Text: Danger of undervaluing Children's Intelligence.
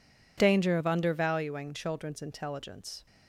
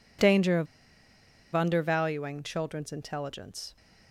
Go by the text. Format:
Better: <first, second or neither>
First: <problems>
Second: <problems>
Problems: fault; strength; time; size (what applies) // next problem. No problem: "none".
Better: first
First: none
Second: pauses between "of" and "undervaluing"; noticeable; at 0.6 s; 0.87 s long